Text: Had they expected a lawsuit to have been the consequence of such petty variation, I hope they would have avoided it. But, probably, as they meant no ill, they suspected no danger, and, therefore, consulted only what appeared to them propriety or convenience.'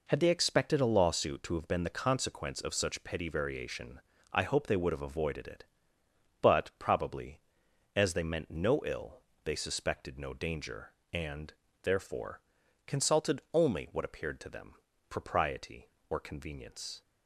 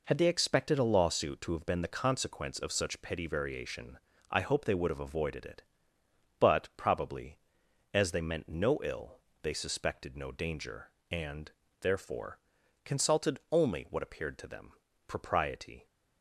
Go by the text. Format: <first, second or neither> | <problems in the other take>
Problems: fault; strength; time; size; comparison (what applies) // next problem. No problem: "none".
first | pauses between "them" and "propriety"; slight; at 14.7 s; 0.34 s long; slight in the first // stops before "or convenience"; at 15.8 s